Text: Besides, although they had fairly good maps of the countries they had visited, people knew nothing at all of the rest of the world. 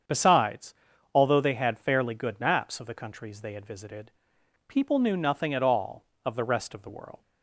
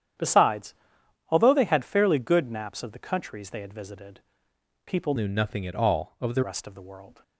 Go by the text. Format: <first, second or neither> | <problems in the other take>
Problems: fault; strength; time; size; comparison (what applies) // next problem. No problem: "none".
first | starts louder than the rest; strong; until 1.7 s; 10 dB; strong in the first // changes voice from "knew" to "the"; from 5.1 to 6.4 s; 1.3 s long